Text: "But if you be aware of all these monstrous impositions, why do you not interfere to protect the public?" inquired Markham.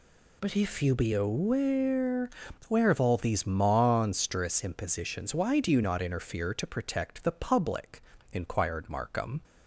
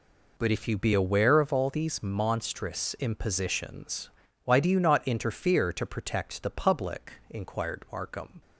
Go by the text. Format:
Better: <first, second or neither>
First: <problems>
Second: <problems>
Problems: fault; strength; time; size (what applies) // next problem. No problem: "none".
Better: second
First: says "aware" twice; at 2.6 s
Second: none